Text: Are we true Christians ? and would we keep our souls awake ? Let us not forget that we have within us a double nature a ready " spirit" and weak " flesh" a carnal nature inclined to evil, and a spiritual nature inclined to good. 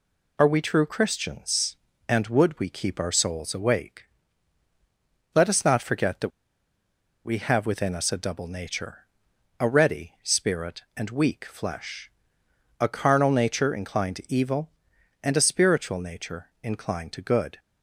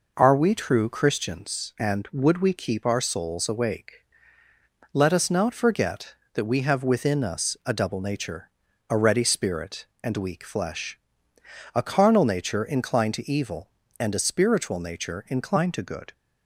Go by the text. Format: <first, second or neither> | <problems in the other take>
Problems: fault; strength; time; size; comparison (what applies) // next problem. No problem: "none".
second | pauses between "that" and "we"; noticeable; at 6.3 s; 0.96 s long // pauses between "nature" and "a"; noticeable; at 9.0 s; 0.54 s long; also in the second // pauses between "flesh" and "a"; noticeable; at 12.0 s; 0.70 s long; noticeable in the second